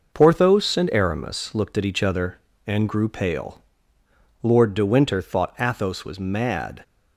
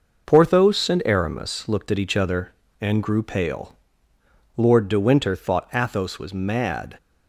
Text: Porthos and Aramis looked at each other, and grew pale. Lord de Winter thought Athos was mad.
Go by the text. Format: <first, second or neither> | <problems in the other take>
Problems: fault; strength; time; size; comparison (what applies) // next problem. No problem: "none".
neither | none